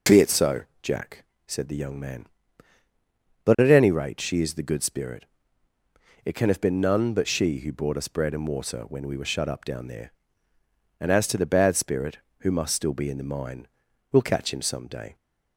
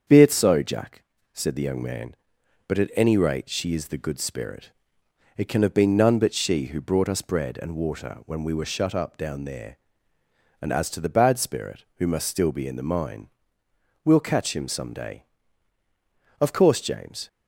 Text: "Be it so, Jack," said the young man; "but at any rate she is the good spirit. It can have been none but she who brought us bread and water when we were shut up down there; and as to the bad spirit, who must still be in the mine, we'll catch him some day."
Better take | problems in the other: first | starts louder than the rest; strong; until 1.3 s; 7 dB // goes on to say "Of course James"; noticeable; from 16.3 s on; 0.88 s long

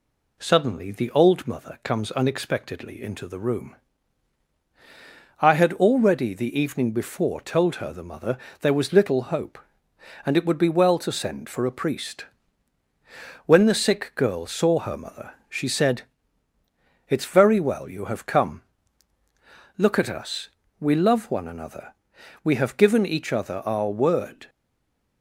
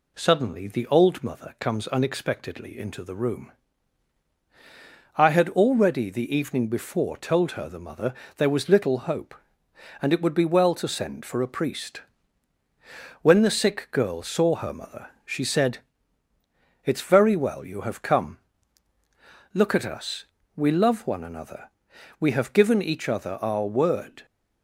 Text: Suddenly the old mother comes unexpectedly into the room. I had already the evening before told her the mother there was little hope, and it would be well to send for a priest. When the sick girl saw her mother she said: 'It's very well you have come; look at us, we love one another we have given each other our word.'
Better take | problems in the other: second | pauses between "mother" and "there"; slight; at 8.3 s; 0.24 s long; slight in the second // pauses between "mother" and "she"; slight; at 15.3 s; 0.16 s long; slight in the second // pauses between "another" and "we"; noticeable; at 21.9 s; 0.50 s long; noticeable in the second // stays silent after the last word; slight; from 24.4 s on; 0.8 s long

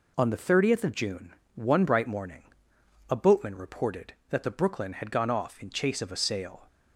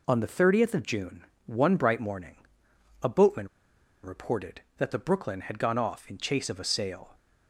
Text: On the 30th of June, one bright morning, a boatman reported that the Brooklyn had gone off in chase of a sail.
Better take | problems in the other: first | pauses between "boatman" and "reported"; noticeable; at 3.4 s; 0.55 s long

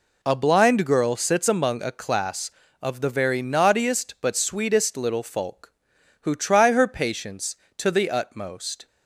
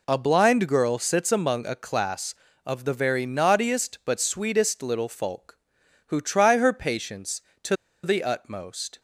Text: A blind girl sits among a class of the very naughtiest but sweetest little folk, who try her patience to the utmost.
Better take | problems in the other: first | pauses between "to" and "the"; slight; at 7.7 s; 0.29 s long

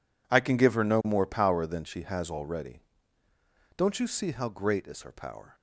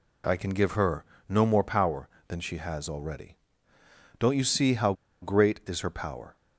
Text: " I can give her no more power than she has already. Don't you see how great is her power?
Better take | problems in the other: first | pauses between "her" and "no"; slight; at 1.0 s; 0.24 s long // pauses between "how" and "great"; slight; at 4.9 s; 0.28 s long

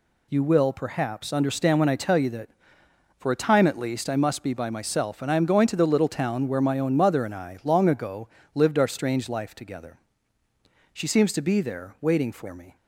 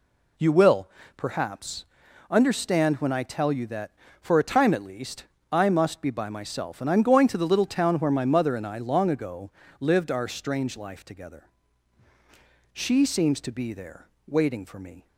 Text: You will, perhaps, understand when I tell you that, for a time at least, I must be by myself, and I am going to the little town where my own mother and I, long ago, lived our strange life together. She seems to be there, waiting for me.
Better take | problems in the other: first | skips "own"; at 8.2 s

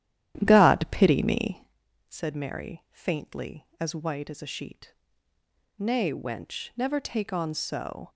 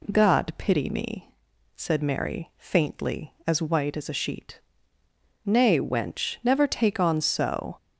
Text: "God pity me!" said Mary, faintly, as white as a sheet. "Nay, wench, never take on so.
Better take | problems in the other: second | starts louder than the rest; strong; until 1.8 s; 11.5 dB

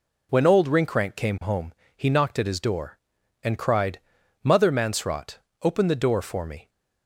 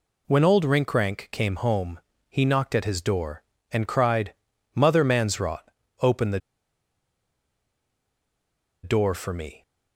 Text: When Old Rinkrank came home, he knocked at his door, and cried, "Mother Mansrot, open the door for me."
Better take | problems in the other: first | pauses between "the" and "door"; strong; at 6.3 s; 2.4 s long

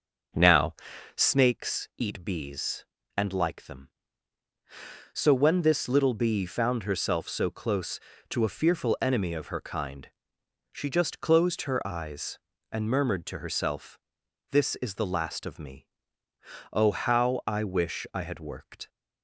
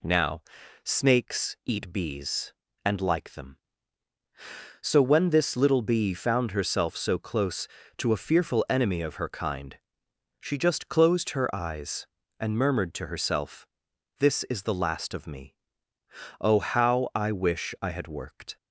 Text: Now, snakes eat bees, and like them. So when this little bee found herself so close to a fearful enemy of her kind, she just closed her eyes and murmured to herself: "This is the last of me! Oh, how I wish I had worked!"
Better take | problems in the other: second | starts louder than the rest; until 1.4 s; 6 dB

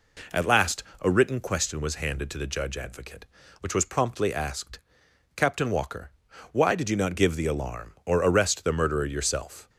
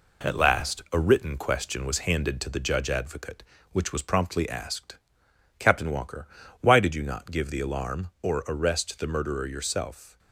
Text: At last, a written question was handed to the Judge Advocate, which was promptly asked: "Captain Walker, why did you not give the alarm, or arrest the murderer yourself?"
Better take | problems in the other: first | gets quieter; noticeable; throughout; 4.5 dB

